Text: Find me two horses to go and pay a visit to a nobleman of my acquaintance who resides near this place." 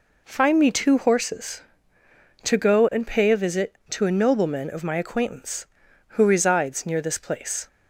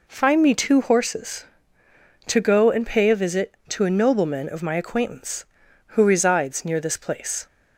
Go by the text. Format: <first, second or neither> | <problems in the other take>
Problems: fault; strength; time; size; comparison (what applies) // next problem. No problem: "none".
neither | none